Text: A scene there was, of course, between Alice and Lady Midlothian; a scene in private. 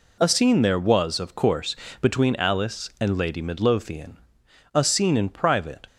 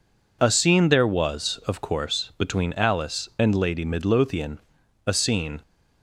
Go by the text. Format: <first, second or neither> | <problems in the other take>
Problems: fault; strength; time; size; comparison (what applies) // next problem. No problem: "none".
first | stops before "in private"; at 5.6 s